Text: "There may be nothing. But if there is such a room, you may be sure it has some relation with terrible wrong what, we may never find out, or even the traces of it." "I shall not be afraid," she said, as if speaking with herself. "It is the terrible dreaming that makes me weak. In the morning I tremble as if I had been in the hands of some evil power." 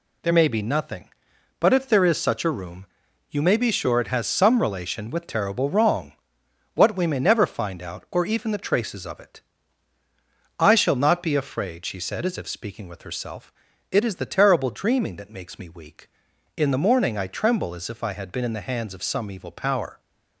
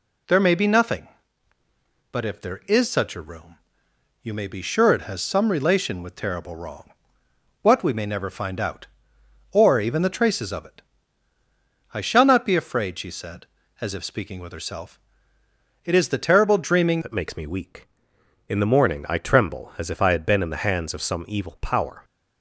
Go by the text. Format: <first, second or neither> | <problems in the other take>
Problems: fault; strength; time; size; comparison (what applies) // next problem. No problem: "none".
first | pauses between "wrong" and "what"; noticeable; at 6.9 s; 0.70 s long; noticeable in the first // changes voice at "that"; from 17.0 s on; 5.0 s long